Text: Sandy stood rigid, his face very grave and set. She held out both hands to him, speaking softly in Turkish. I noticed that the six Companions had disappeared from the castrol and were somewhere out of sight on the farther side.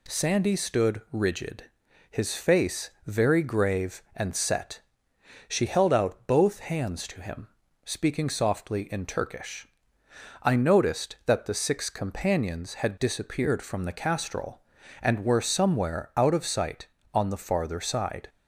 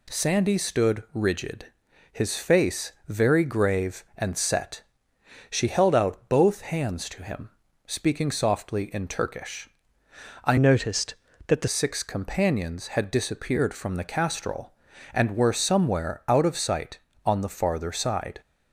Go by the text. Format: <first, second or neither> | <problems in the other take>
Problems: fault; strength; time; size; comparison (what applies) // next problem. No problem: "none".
first | changes voice from "noticed" to "the"; from 10.5 to 11.6 s; 1.1 s long